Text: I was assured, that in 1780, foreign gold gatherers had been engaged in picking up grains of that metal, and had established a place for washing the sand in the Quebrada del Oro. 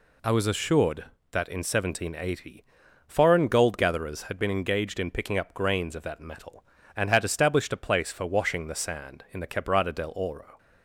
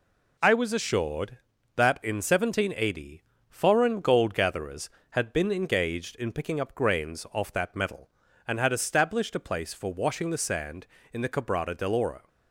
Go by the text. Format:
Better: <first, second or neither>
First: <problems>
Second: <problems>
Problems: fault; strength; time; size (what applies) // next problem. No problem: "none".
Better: first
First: none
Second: says "off" for "of"; at 7.3 s